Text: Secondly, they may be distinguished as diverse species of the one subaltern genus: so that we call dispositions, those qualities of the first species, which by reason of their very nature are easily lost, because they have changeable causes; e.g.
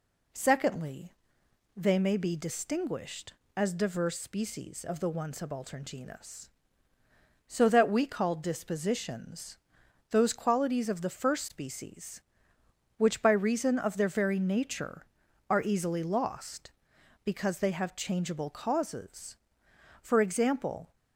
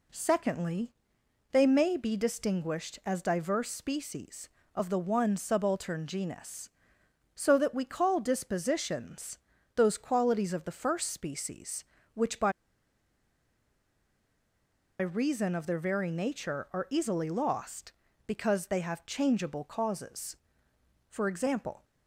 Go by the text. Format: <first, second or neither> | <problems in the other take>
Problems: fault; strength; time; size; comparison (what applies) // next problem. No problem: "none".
first | pauses between "by" and "reason"; strong; at 12.5 s; 2.4 s long